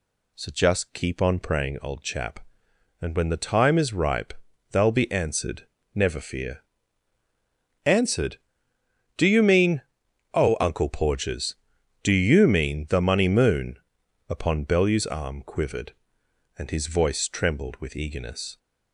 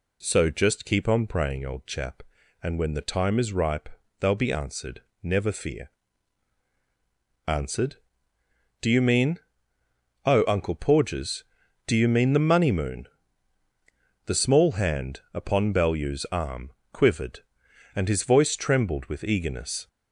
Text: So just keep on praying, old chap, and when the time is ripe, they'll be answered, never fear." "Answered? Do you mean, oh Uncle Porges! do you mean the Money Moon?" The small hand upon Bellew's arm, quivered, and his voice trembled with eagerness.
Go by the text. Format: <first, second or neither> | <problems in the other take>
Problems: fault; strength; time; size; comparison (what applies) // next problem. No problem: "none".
second | skips "The small hand"; at 14.0 s